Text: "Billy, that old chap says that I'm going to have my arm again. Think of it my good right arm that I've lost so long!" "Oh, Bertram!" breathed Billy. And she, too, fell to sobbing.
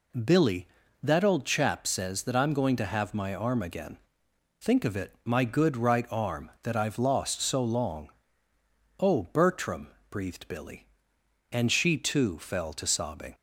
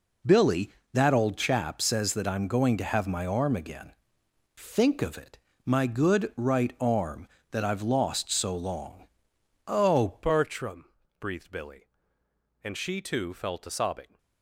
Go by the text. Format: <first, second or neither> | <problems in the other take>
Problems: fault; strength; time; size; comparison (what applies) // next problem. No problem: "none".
first | pauses between "it" and "my"; slight; at 5.3 s; 0.26 s long // changes voice at "Bertram"; from 10.2 s on; 3.9 s long